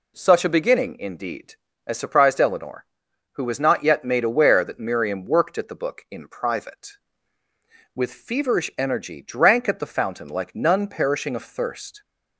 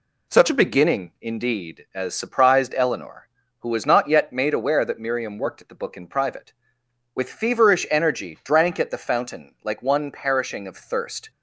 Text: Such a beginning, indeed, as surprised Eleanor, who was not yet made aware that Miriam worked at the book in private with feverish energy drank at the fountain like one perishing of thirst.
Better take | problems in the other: second | says "none" for "one"; at 10.5 s

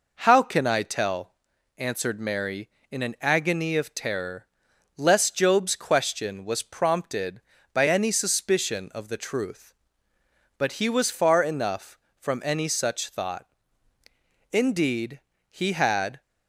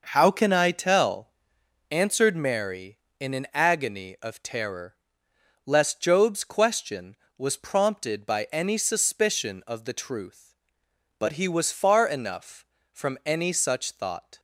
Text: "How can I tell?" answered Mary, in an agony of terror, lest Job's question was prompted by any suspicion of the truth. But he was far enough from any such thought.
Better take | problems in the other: second | goes on to say "Indeed he had"; strong; from 14.5 s on; 1.6 s long

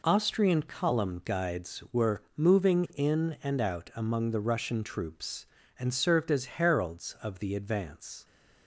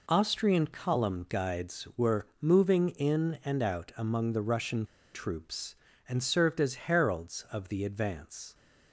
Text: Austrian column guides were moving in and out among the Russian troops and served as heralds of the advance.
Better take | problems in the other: first | pauses between "Russian" and "troops"; slight; at 4.8 s; 0.30 s long

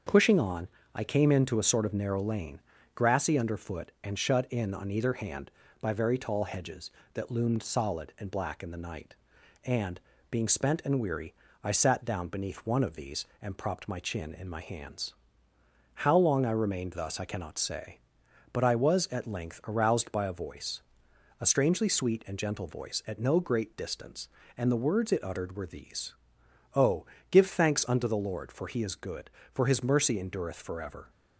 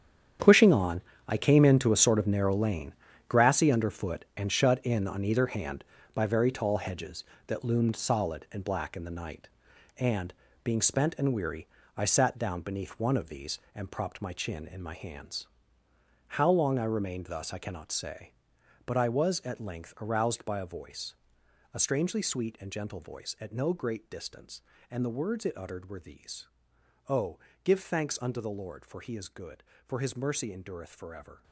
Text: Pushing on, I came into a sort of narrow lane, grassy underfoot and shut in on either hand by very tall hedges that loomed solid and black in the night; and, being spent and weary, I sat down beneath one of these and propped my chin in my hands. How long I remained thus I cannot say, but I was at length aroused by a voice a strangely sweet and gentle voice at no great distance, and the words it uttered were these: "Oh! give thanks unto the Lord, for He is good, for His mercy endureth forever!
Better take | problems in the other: first | gets quieter; strong; throughout; 12.5 dB // starts louder than the rest; strong; until 1.6 s; 9 dB; also in the first // pauses between "voice" and "a"; noticeable; at 21.1 s; 0.58 s long; noticeable in the first

